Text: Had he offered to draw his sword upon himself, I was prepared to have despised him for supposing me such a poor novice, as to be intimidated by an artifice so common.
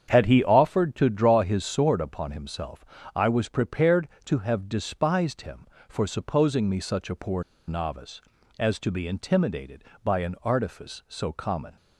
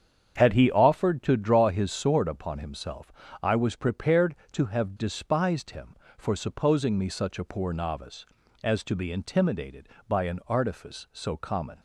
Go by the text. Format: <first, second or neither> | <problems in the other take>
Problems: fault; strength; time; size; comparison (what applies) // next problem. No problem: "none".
second | starts louder than the rest; strong; until 1.1 s; 8 dB; strong in the second // pauses between "poor" and "novice"; slight; at 7.4 s; 0.24 s long